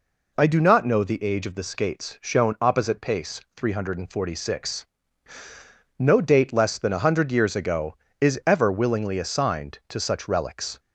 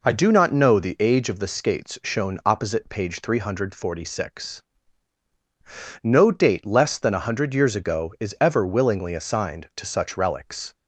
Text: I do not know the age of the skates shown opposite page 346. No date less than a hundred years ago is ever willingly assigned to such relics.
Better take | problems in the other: second | says "pace" for "page"; at 3.0 s

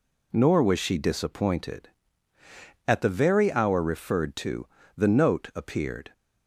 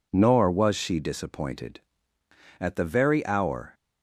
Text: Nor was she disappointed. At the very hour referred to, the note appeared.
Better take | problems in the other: first | stops before "referred to the note appeared"; at 3.7 s

